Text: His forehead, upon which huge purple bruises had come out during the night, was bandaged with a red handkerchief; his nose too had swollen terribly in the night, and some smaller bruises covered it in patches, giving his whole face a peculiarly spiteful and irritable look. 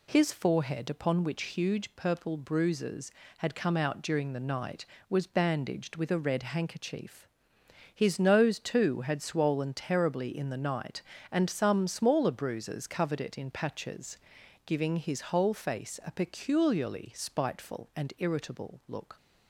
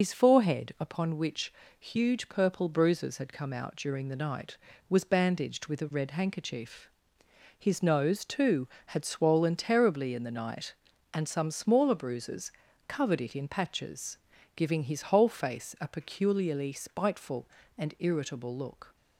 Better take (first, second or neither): first